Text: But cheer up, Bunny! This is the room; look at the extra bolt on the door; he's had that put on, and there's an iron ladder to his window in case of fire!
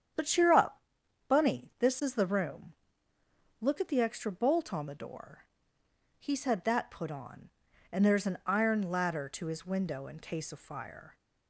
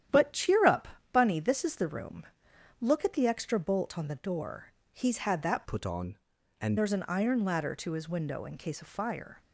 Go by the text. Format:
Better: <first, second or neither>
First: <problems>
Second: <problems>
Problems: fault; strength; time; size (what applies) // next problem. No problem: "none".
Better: first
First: starts louder than the rest; strong; until 1.6 s; 8.5 dB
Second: starts louder than the rest; strong; until 1.3 s; 10.5 dB // changes voice from "put" to "and"; from 5.6 to 6.7 s; 1.1 s long